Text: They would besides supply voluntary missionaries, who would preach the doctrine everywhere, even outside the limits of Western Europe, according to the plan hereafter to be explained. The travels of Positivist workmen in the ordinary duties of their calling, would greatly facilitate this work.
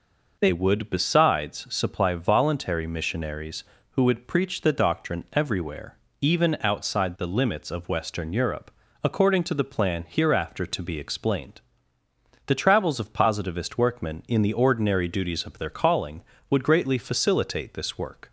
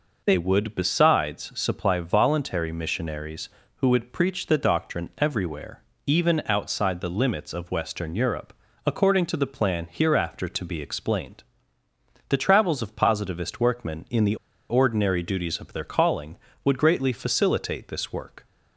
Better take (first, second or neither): first